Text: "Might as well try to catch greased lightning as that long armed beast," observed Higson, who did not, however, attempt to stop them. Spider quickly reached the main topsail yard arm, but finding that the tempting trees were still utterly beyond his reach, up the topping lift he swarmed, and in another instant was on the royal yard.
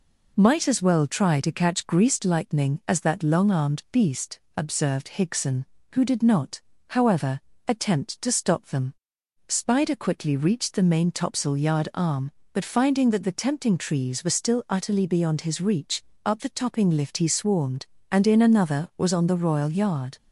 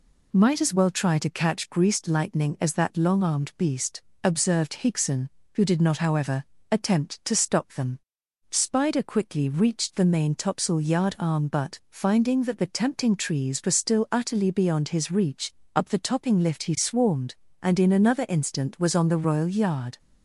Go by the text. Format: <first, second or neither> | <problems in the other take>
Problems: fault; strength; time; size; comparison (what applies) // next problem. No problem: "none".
second | skips "instant"; at 18.9 s